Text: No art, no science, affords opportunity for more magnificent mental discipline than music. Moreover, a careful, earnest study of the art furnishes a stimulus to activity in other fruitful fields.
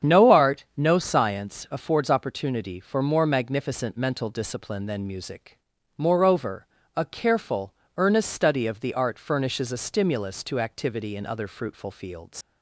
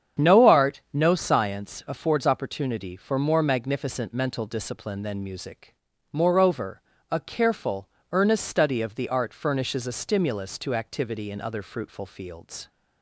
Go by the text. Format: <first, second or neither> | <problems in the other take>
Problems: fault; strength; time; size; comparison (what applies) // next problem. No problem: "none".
second | starts louder than the rest; strong; until 1.1 s; 8 dB; strong in the second // leaves "fields" unfinished; at 12.4 s; 110 ms